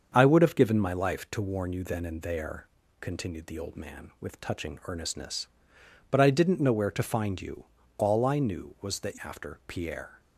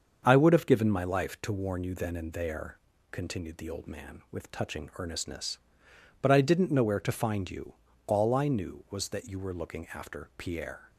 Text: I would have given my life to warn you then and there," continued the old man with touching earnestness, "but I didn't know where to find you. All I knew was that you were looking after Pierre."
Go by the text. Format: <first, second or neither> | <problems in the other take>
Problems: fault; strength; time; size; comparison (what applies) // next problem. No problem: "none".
second | starts louder than the rest; until 1.1 s; 7 dB; also in the second // skips "you were looking"; at 9.1 s